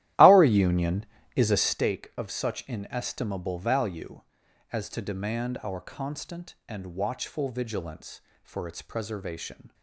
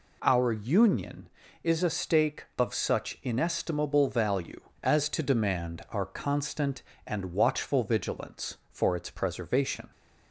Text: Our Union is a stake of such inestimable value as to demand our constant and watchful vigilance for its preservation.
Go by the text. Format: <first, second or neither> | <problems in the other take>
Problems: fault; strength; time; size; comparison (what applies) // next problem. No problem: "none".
second | starts louder than the rest; strong; until 1.9 s; 14 dB